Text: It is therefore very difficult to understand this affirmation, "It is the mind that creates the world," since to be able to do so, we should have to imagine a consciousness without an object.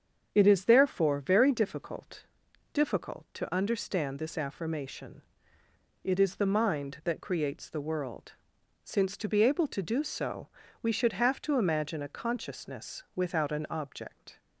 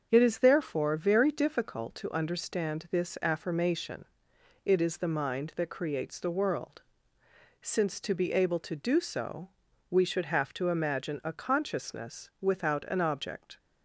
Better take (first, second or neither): second